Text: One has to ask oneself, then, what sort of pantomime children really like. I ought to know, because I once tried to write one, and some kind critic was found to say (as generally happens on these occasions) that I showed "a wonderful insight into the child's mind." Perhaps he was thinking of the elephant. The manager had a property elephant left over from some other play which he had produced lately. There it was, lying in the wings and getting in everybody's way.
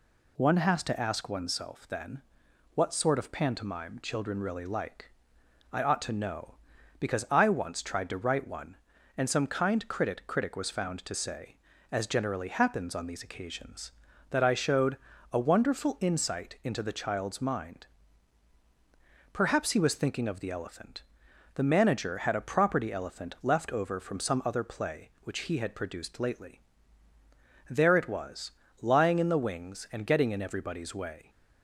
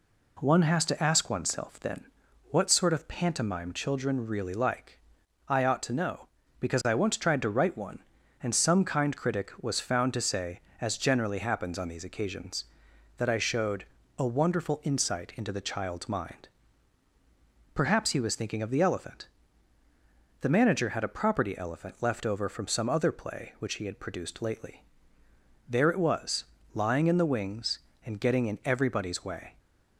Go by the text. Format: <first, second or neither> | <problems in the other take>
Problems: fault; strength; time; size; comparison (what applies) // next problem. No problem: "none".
second | says "critic" twice; at 10.2 s // pauses between "showed" and "a"; slight; at 14.9 s; 0.34 s long; slight in the second